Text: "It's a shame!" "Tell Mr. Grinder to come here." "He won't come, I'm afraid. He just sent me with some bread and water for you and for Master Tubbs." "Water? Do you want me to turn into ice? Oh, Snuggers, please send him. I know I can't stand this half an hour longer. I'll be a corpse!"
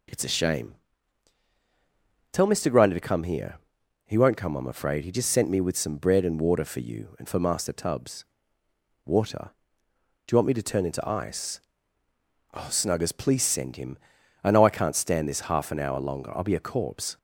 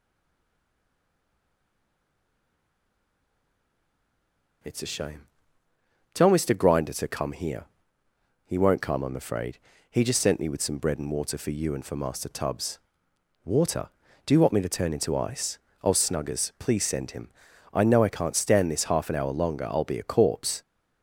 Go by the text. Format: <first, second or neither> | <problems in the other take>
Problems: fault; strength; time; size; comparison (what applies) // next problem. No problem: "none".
first | stays silent before the first word; strong; until 4.6 s; 4.6 s long